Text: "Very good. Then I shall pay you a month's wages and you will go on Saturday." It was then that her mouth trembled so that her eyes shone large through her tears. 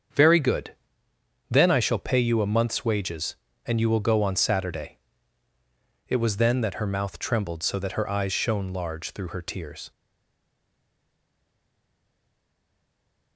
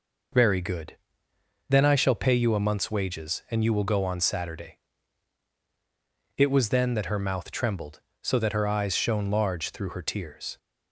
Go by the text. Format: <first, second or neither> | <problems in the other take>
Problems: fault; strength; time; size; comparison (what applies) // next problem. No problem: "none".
second | starts louder than the rest; strong; until 1.8 s; 7.5 dB // stays silent after the last word; strong; from 9.9 s on; 3.4 s long